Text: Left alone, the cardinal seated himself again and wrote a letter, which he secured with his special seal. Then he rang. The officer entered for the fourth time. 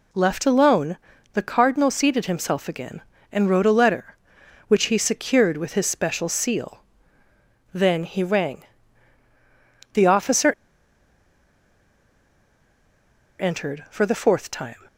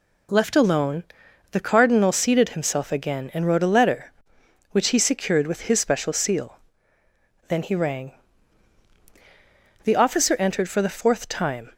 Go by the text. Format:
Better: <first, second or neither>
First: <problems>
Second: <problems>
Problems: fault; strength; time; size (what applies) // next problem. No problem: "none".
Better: second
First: pauses between "officer" and "entered"; strong; at 10.5 s; 2.8 s long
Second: none